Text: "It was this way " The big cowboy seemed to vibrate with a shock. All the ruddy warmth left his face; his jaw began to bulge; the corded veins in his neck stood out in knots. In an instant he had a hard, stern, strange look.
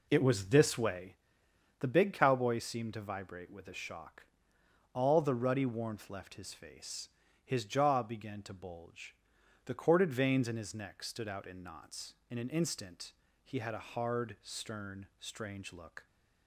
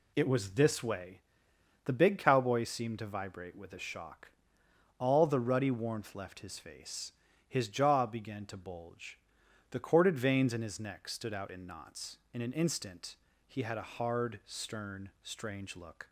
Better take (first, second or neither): second